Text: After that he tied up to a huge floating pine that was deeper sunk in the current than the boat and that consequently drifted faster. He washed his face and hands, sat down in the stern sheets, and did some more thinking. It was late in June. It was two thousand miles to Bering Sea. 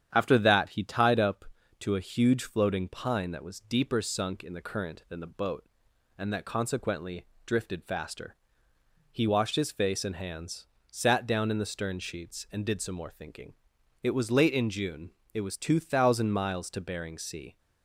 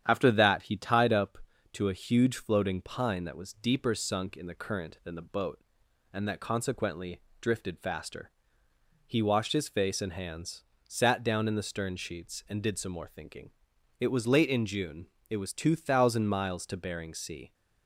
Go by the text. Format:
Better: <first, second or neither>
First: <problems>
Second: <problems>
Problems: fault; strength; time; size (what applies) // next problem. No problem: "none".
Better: neither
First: starts louder than the rest; strong; until 1.1 s; 9 dB // pauses between "consequently" and "drifted"; slight; at 7.2 s; 0.20 s long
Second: starts louder than the rest; strong; until 1.0 s; 9 dB // pauses between "consequently" and "drifted"; slight; at 7.2 s; 0.20 s long